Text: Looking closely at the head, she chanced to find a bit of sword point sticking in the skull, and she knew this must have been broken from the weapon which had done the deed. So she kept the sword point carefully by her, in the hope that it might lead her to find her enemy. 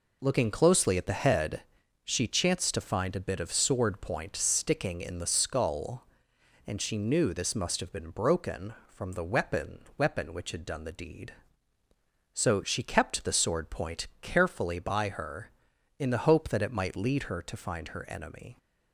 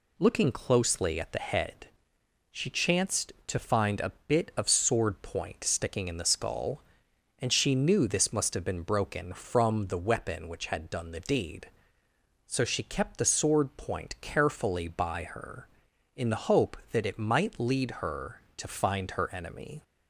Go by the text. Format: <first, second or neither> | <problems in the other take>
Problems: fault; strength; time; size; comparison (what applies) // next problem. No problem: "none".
second | says "weapon" twice; at 9.9 s